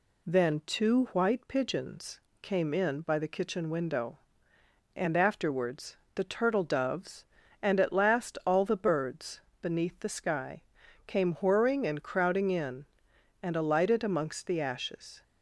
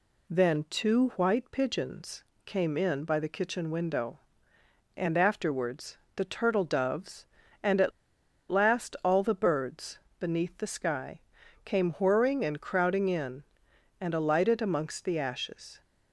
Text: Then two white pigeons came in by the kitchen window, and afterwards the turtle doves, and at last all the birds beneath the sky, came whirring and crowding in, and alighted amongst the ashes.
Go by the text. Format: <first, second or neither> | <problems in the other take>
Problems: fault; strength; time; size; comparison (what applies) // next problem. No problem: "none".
first | pauses between "pigeons" and "came"; slight; at 2.2 s; 0.20 s long; slight in the first // pauses between "afterwards" and "the"; slight; at 5.9 s; 0.20 s long; slight in the first // pauses between "at" and "last"; noticeable; at 7.9 s; 0.59 s long // pauses between "birds" and "beneath"; slight; at 9.9 s; 0.22 s long; slight in the first